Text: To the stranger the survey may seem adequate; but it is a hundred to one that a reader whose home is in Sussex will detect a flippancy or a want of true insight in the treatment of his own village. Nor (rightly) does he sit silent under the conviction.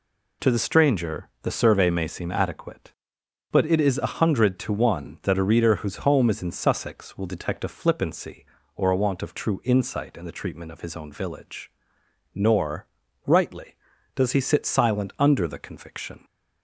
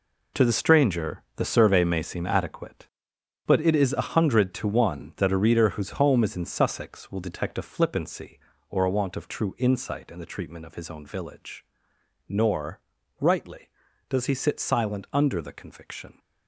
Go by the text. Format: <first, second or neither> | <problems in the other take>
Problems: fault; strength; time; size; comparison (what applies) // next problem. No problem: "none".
first | gets quieter; strong; throughout; 10 dB